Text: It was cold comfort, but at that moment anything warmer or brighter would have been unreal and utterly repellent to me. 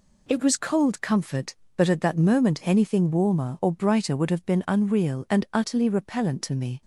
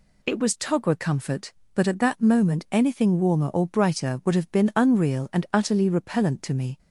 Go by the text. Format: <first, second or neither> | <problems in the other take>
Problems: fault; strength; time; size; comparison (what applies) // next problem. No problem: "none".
first | says "togwa" for "cold"; at 0.5 s